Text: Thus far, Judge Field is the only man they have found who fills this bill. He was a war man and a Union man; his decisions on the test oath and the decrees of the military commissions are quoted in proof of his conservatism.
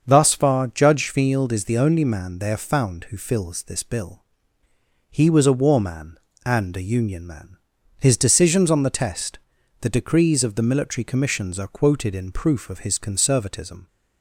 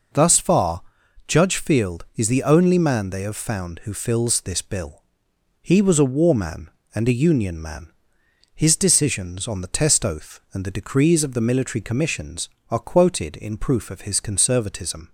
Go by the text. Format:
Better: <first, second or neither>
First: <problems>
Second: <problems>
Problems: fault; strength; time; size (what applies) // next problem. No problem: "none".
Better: second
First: starts louder than the rest; until 1.0 s; 6.5 dB // skips "oath and"; at 9.5 s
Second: none